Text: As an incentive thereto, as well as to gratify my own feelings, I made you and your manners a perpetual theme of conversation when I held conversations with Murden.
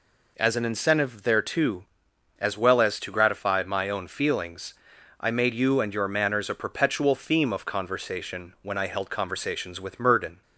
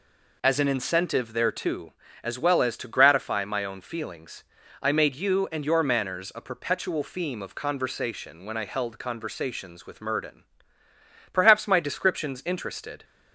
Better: first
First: none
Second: goes on to say "Perhaps my descriptions interested"; strong; from 11.3 s on; 1.7 s long

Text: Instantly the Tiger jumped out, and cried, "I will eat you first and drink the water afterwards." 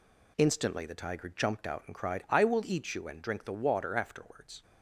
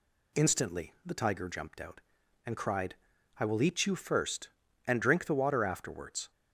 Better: second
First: skips "first"; at 3.0 s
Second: none

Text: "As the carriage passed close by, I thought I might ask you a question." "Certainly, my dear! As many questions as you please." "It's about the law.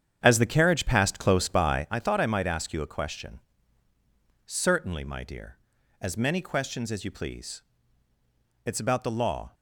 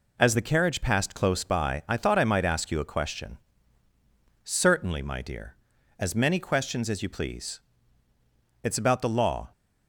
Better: second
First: starts louder than the rest; strong; until 1.9 s; 8.5 dB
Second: none

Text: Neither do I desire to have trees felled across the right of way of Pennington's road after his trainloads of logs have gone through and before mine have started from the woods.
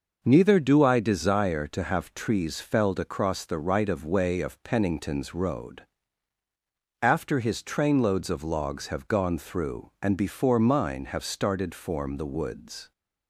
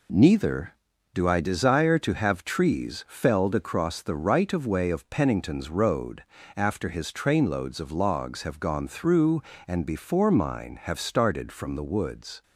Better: second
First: pauses between "road" and "after"; at 5.8 s; 1.2 s long // says "form" for "from"; at 11.7 s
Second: pauses between "road" and "after"; slight; at 6.2 s; 0.32 s long

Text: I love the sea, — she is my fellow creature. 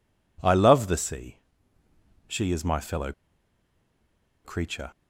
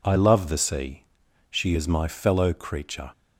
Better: second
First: pauses between "fellow" and "creature"; strong; at 3.1 s; 1.3 s long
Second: none

